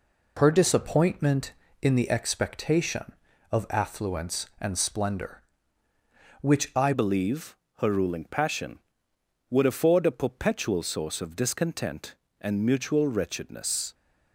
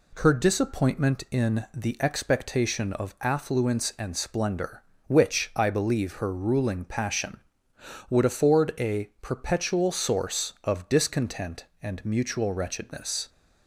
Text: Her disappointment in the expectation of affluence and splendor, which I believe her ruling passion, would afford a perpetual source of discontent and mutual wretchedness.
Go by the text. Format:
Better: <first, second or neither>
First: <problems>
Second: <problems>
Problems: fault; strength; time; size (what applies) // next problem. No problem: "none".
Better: second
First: changes voice at "believe"; from 6.9 s on; 7.0 s long // pauses between "believe" and "her"; slight; at 7.5 s; 0.22 s long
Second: none